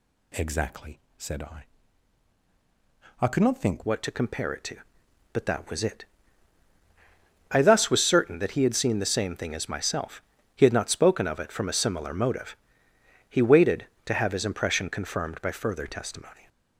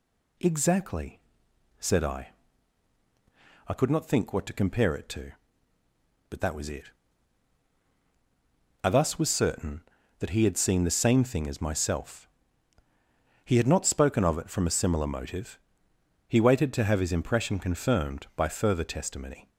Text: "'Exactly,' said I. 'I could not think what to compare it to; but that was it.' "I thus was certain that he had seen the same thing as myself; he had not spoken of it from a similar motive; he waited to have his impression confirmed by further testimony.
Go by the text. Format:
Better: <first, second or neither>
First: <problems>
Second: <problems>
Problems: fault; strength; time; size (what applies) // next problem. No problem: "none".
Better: second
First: changes voice at "what"; from 3.8 s on; 12.6 s long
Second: none